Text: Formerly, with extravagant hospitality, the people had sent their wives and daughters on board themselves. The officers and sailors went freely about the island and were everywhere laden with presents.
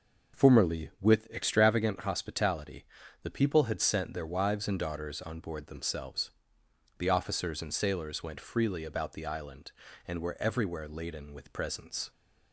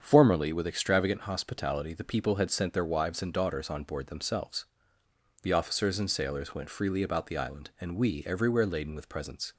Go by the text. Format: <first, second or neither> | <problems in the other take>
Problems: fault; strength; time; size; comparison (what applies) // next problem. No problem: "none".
first | starts louder than the rest; strong; until 1.0 s; 7.5 dB // says "we" for "were"; at 7.9 s